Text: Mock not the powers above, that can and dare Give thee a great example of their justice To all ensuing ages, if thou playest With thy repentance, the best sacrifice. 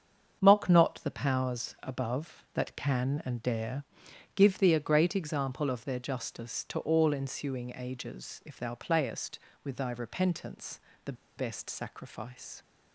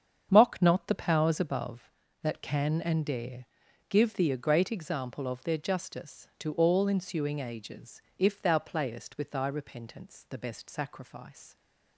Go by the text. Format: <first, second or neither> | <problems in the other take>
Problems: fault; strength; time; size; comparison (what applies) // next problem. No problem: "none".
second | starts louder than the rest; strong; until 1.4 s; 7 dB; strong in the second // pauses between "dare" and "Give"; noticeable; at 3.8 s; 0.52 s long; also in the second // pauses between "the" and "best"; slight; at 11.1 s; 0.23 s long